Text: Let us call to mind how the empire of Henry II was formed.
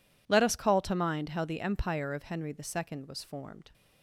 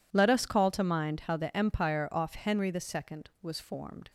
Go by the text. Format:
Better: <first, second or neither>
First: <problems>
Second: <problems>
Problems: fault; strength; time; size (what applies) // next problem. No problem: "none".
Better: first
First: none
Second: says "off" for "of"; at 2.1 s